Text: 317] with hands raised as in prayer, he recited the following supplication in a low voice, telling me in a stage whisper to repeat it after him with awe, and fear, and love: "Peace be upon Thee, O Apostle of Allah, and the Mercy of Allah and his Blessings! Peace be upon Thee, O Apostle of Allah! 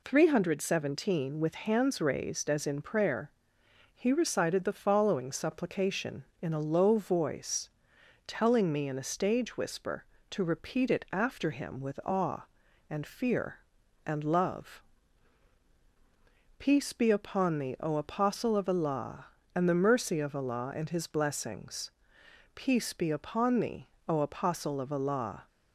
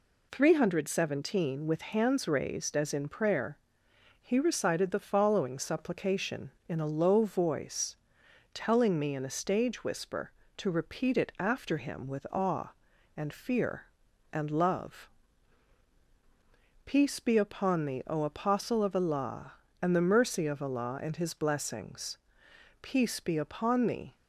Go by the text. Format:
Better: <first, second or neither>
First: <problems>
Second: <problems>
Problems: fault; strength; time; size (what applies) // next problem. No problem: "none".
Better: first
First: none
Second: stops before "O Apostle of Allah"; at 24.1 s